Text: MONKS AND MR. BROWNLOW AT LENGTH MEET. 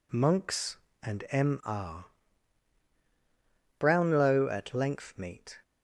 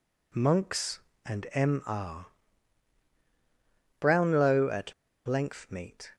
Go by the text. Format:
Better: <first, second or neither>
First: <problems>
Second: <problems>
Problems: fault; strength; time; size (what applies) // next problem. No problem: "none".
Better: first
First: none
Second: pauses between "AT" and "LENGTH"; slight; at 4.9 s; 0.33 s long